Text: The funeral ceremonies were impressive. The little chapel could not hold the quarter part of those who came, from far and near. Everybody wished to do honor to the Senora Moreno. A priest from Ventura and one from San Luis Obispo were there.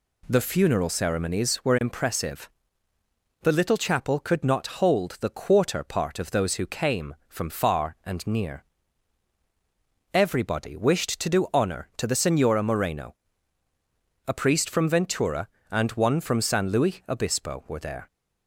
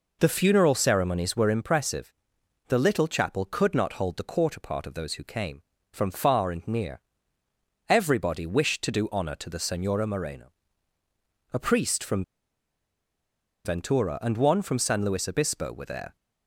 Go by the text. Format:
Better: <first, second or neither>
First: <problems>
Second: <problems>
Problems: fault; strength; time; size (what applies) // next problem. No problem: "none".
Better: first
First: none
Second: pauses between "from" and "Ventura"; strong; at 12.2 s; 1.4 s long